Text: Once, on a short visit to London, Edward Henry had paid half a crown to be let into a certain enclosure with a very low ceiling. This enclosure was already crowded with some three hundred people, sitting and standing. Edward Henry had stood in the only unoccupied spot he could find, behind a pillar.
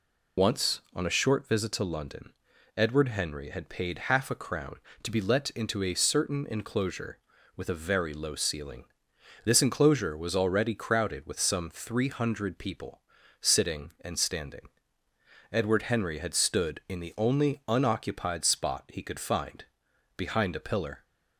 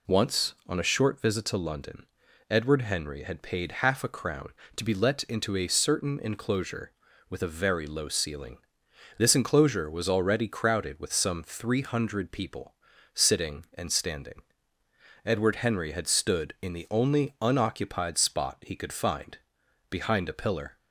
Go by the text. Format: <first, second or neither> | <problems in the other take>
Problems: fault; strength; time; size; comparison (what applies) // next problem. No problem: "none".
second | loses the start of "Once"; at 0.3 s; 40 ms